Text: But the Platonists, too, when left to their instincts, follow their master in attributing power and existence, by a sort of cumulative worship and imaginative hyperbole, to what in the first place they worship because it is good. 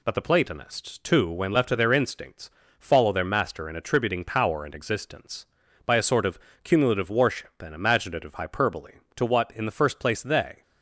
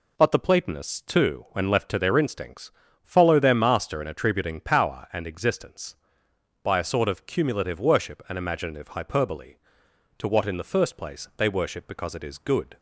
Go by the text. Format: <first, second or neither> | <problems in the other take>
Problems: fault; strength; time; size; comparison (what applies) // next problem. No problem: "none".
second | pauses between "of" and "cumulative"; slight; at 6.3 s; 0.26 s long // stops before "worship because it is good"; at 10.6 s